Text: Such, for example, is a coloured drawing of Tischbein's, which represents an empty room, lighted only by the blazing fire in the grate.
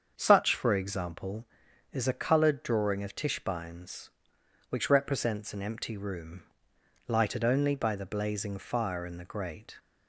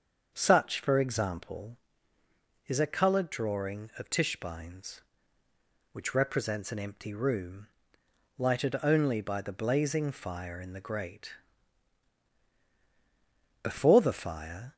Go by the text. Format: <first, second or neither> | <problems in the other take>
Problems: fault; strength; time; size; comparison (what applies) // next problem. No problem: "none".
first | starts louder than the rest; until 1.3 s; 7 dB; also in the first // goes on to say "Before the fire"; noticeable; from 13.6 s on; 1.1 s long